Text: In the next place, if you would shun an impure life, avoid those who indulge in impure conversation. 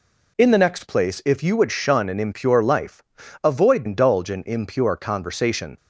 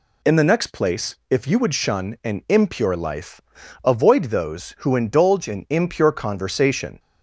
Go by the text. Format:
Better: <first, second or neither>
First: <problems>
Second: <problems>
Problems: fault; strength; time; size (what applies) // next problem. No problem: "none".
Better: second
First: skips "those who"; at 3.8 s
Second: none